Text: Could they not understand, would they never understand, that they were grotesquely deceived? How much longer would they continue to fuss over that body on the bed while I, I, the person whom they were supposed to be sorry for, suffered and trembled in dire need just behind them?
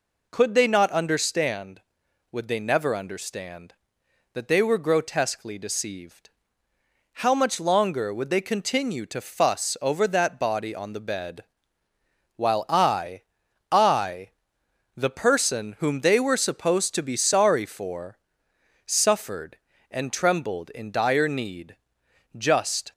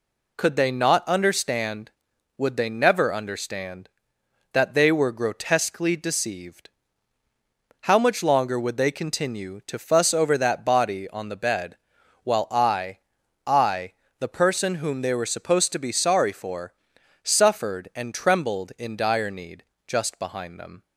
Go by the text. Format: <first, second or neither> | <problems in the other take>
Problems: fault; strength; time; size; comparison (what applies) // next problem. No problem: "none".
second | pauses between "bed" and "while"; noticeable; at 11.4 s; 0.92 s long; noticeable in the second // pauses between "need" and "just"; noticeable; at 21.7 s; 0.60 s long; slight in the second // stops before "behind them"; at 22.9 s